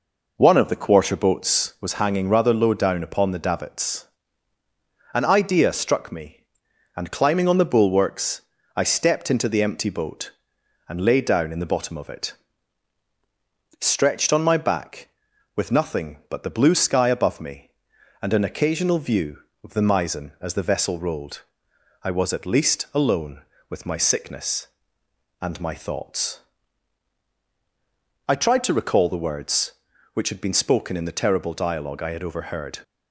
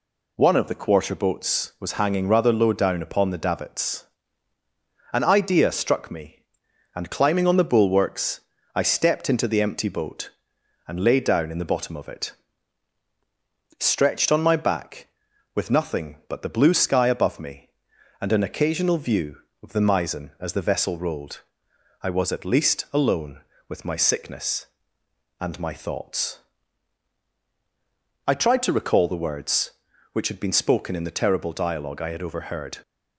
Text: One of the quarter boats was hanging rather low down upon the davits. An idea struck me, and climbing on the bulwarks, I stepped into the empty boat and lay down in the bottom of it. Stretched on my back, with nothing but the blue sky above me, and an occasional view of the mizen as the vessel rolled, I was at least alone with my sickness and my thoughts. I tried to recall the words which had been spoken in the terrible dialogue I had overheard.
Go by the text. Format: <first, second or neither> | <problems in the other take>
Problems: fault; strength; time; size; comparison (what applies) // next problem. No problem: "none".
second | starts louder than the rest; noticeable; until 1.9 s; 5 dB